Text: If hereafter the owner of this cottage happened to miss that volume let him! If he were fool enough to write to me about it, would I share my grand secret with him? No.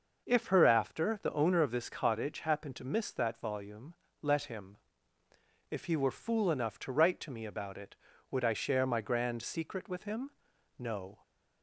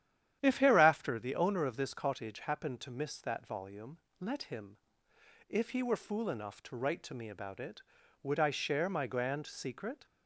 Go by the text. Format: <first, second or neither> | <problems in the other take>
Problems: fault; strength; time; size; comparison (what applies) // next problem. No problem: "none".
first | starts louder than the rest; strong; until 1.4 s; 10.5 dB // pauses between "volume" and "let"; slight; at 3.9 s; 0.24 s long; slight in the first // stops before "with him No"; at 10.0 s